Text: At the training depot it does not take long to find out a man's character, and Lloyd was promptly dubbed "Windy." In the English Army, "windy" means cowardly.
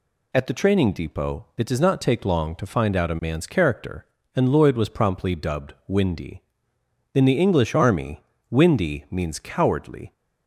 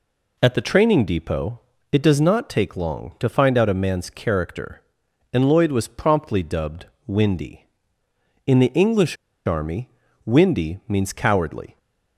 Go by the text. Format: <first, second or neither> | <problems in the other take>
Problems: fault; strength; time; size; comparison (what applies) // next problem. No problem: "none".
first | pauses between "depot" and "it"; slight; at 1.5 s; 0.30 s long // pauses between "dubbed" and "Windy"; slight; at 6.8 s; 0.22 s long // pauses between "English" and "Army"; slight; at 9.1 s; 0.31 s long